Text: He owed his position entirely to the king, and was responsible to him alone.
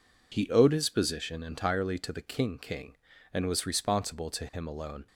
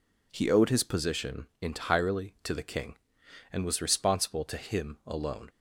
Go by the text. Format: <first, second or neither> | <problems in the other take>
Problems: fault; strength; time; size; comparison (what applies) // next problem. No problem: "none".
second | says "king" twice; at 2.5 s